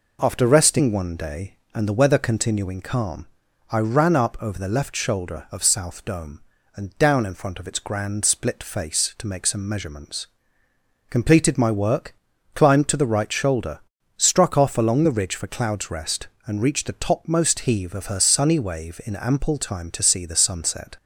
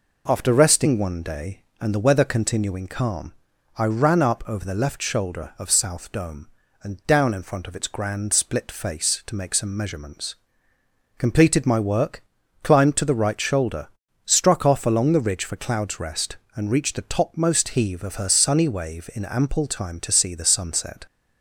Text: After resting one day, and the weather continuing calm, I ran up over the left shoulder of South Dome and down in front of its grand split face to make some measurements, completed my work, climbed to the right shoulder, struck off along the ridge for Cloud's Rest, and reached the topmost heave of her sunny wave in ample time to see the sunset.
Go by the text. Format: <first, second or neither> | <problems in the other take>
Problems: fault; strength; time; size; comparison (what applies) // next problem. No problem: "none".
neither | none